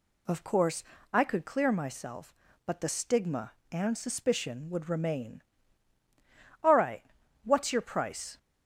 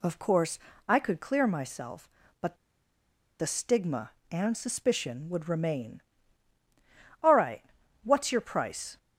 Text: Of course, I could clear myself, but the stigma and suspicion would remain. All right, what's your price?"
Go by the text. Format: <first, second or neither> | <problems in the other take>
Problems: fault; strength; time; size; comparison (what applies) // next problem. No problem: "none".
first | pauses between "but" and "the"; noticeable; at 2.5 s; 0.82 s long